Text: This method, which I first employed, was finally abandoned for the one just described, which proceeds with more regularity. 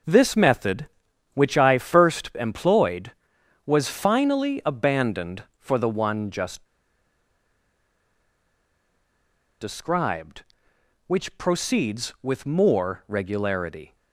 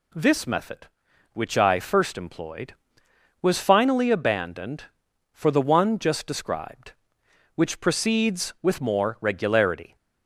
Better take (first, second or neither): second